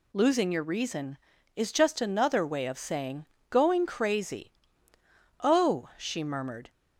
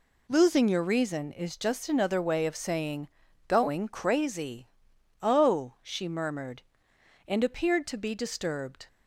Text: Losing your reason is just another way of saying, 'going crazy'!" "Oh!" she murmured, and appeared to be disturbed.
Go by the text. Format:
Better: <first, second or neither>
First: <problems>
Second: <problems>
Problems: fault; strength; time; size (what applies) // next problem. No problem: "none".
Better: second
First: stops before "and appeared to be disturbed"; at 6.6 s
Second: none